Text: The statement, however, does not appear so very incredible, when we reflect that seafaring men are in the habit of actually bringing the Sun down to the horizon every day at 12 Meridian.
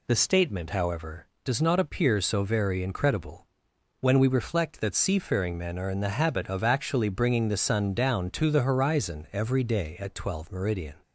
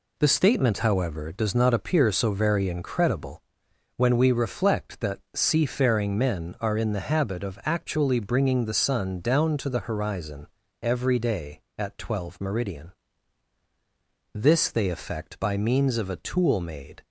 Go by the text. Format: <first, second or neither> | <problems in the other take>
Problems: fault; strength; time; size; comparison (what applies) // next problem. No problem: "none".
first | pauses between "horizon" and "every"; slight; at 10.4 s; 0.34 s long // goes on to say "This they effect by means of a tool made"; strong; from 14.3 s on; 2.7 s long